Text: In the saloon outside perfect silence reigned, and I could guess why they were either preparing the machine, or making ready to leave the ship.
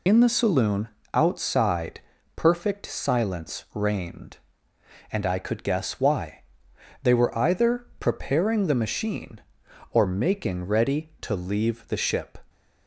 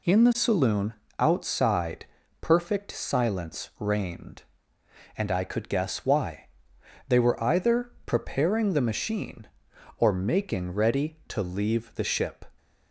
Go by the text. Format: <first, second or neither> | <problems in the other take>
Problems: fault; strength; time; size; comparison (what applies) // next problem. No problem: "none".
second | loses the start of "In"; at 0.0 s; 50 ms // pauses between "saloon" and "outside"; slight; at 0.8 s; 0.26 s long; slight in the second // pauses between "outside" and "perfect"; at 1.9 s; 0.38 s long; also in the second // pauses between "why" and "they"; noticeable; at 6.4 s; 0.60 s long; noticeable in the second // pauses between "either" and "preparing"; slight; at 7.8 s; 0.15 s long